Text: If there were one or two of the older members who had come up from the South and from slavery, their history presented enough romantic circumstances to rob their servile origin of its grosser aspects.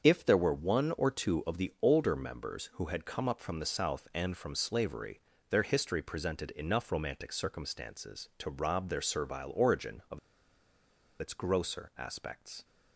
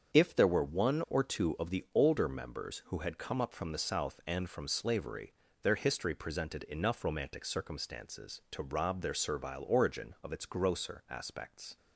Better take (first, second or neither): second